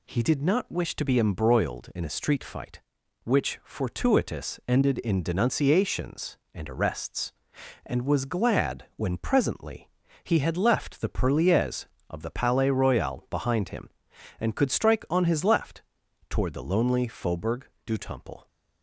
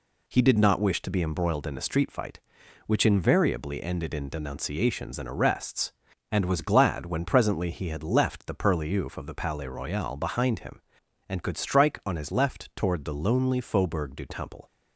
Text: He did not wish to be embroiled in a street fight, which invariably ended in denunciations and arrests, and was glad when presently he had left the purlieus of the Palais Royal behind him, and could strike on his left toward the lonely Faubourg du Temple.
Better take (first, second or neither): second